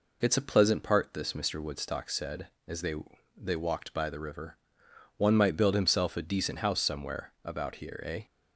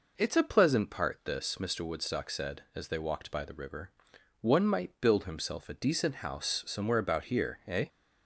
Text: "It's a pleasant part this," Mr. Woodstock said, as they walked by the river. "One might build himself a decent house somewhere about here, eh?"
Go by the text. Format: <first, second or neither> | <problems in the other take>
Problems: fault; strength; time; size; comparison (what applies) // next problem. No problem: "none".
second | says "they" twice; at 3.3 s